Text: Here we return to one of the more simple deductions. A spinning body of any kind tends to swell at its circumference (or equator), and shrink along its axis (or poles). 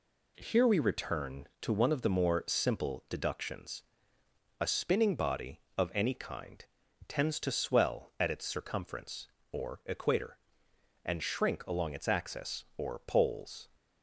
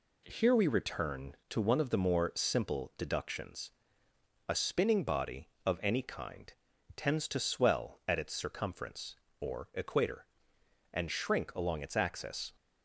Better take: first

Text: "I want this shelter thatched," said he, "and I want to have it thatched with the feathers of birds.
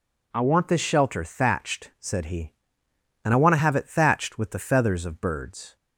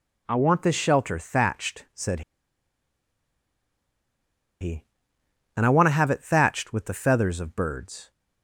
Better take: first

